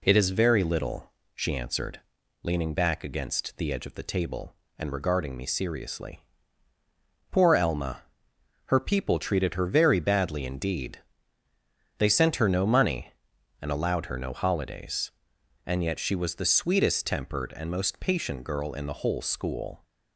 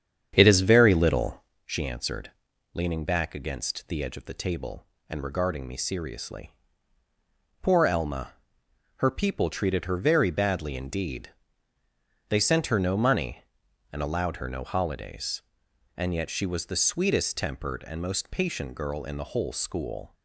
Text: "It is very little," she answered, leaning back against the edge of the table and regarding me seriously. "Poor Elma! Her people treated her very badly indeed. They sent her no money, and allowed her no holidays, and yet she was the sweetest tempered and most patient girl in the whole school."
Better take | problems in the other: first | starts louder than the rest; strong; until 1.5 s; 8.5 dB

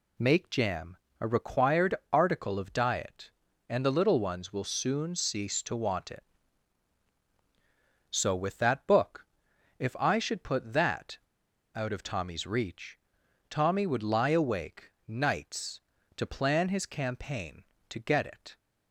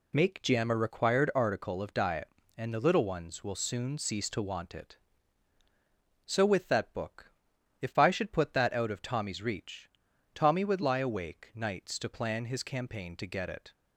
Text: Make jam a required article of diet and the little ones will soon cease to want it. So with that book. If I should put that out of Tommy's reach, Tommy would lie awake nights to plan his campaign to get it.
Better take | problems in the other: second | pauses between "jam" and "a"; slight; at 0.9 s; 0.24 s long // pauses between "required" and "article"; slight; at 1.9 s; 0.18 s long // pauses between "that" and "out"; noticeable; at 11.1 s; 0.55 s long // pauses between "awake" and "nights"; slight; at 14.9 s; 0.16 s long

